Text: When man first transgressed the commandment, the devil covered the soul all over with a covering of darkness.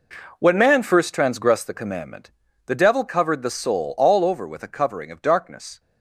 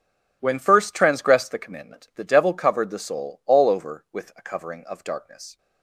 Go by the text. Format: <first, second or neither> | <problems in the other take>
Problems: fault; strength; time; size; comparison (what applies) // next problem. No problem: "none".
first | skips "man"; at 0.5 s